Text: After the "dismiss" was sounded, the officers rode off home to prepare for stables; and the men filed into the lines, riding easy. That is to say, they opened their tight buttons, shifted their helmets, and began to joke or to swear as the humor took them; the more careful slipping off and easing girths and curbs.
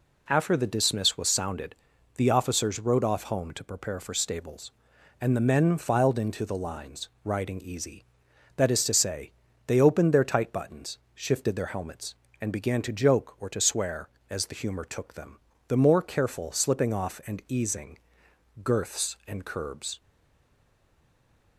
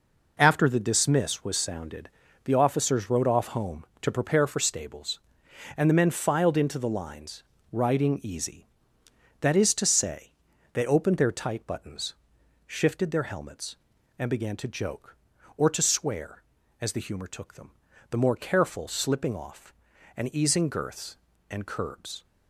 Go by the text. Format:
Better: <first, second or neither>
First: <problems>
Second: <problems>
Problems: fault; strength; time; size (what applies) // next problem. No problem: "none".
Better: second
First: pauses between "easing" and "girths"; noticeable; at 17.9 s; 0.66 s long // stays silent after the last word; noticeable; from 19.9 s on; 1.6 s long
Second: none